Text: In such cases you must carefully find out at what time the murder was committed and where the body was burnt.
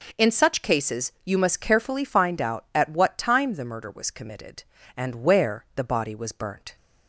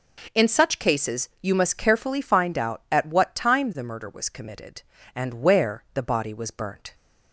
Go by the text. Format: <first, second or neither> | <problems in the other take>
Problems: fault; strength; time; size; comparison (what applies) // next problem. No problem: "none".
neither | none